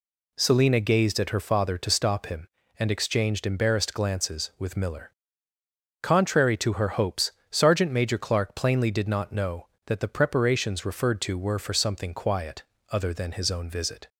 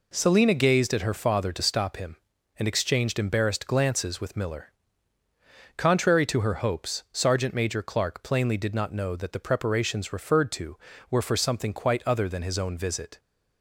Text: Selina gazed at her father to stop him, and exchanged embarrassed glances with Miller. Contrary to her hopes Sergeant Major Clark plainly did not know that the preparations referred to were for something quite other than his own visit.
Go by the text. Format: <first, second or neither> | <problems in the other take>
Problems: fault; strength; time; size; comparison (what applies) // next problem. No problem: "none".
second | pauses between "hopes" and "Sergeant"; slight; at 7.3 s; 0.20 s long // says "quiet" for "quite"; at 12.1 s